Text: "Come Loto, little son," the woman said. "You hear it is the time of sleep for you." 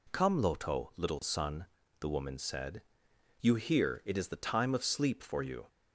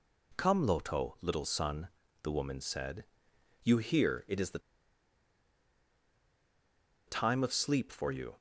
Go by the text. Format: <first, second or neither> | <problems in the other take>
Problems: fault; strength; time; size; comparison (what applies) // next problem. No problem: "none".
first | pauses between "the" and "time"; strong; at 4.5 s; 2.4 s long